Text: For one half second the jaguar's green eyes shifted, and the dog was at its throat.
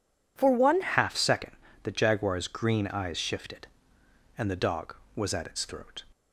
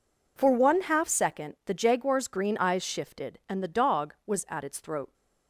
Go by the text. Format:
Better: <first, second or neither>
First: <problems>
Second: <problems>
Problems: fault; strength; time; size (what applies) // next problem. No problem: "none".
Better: second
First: changes voice at "half"; from 0.8 s on; 5.2 s long // pauses between "second" and "the"; slight; at 1.5 s; 0.32 s long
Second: none